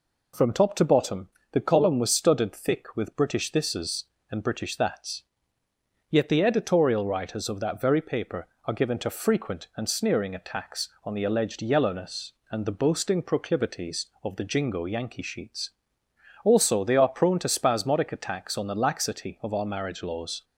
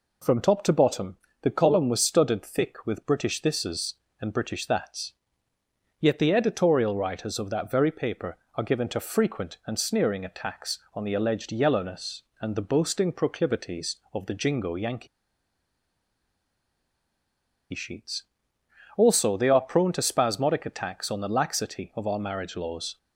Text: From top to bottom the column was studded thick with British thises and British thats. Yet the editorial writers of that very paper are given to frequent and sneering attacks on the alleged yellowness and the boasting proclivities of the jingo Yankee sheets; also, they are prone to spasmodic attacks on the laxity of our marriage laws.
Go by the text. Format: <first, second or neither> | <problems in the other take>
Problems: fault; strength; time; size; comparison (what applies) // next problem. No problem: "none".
first | pauses between "bottom" and "the"; slight; at 1.1 s; 0.24 s long; slight in the first // pauses between "Yankee" and "sheets"; strong; at 15.0 s; 2.6 s long